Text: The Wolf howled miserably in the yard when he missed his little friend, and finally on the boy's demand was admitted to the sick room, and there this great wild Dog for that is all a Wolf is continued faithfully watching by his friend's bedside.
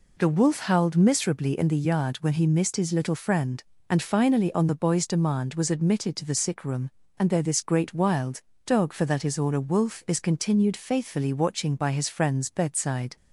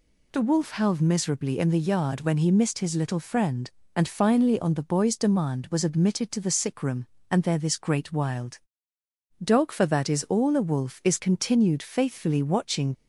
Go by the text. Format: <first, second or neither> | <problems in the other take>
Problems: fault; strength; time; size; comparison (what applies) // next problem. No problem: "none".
first | pauses between "wild" and "Dog"; noticeable; at 8.5 s; 0.84 s long; slight in the first // stops before "by his friend's bedside"; at 12.9 s